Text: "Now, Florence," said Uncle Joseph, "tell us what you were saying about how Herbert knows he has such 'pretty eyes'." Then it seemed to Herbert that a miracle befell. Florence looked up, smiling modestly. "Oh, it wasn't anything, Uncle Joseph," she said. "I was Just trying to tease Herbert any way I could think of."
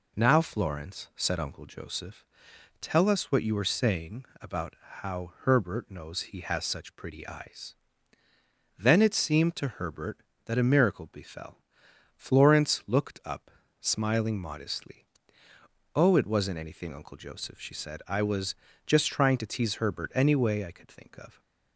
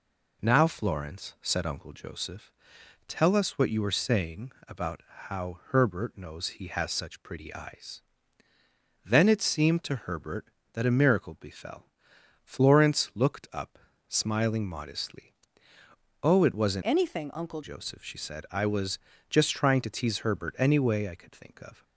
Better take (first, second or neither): first